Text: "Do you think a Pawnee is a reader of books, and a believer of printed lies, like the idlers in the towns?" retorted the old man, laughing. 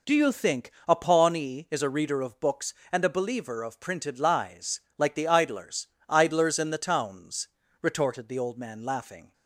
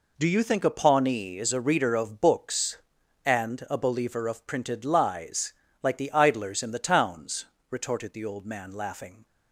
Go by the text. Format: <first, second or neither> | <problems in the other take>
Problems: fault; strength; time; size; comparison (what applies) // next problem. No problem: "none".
second | pauses between "think" and "a"; slight; at 0.7 s; 0.18 s long // says "idlers" twice; at 6.0 s